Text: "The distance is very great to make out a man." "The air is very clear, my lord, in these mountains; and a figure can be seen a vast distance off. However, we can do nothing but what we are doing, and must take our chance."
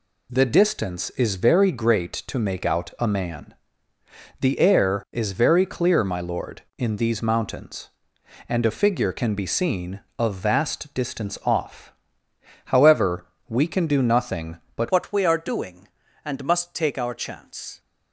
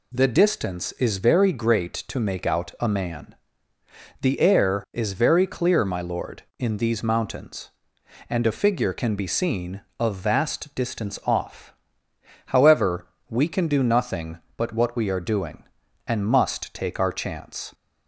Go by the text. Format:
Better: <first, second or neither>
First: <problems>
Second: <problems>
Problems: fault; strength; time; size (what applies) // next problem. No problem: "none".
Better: second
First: changes voice at "what"; from 14.9 s on; 2.8 s long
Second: none